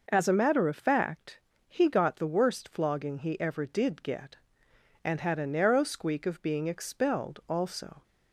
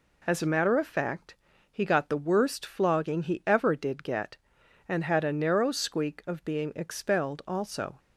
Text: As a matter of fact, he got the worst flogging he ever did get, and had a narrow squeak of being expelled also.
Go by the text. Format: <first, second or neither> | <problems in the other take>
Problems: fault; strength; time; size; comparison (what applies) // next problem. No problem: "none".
neither | none